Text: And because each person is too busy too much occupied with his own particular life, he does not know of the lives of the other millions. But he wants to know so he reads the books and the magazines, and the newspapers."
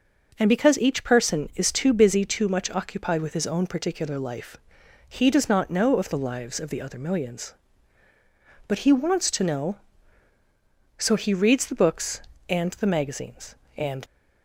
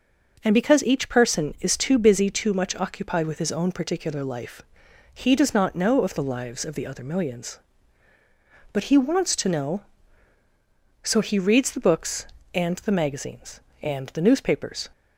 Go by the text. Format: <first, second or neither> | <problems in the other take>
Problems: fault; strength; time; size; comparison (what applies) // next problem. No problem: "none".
second | stops before "the newspapers"; at 14.0 s